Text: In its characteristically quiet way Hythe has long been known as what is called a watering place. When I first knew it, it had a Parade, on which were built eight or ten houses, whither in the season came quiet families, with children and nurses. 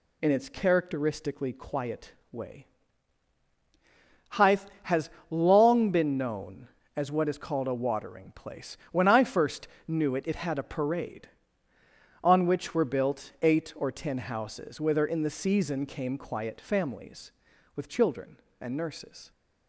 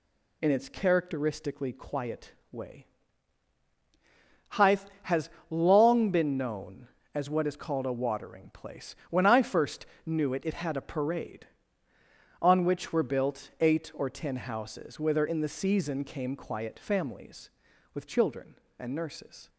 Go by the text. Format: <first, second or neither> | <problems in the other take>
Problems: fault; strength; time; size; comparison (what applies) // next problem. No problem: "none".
neither | pauses between "quiet" and "way"; slight; the same in both // pauses between "way" and "Hythe"; strong; the same in both // pauses between "has" and "long"; slight; the same in both // pauses between "first" and "knew"; slight; the same in both